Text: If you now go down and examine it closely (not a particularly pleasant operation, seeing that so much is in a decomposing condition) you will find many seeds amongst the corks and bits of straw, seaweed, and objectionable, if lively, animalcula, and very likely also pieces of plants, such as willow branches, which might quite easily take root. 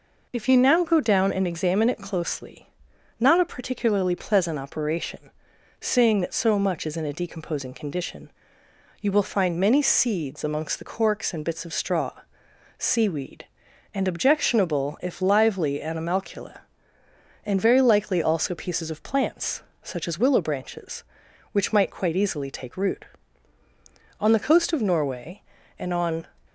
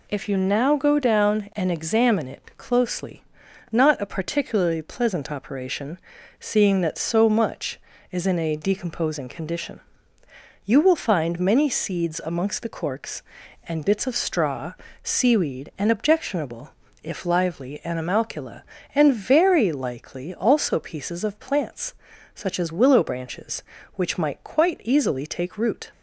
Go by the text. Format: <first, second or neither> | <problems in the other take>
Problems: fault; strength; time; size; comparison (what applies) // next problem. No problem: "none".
second | goes on to say "On the coast of Norway and on"; strong; from 24.1 s on; 2.0 s long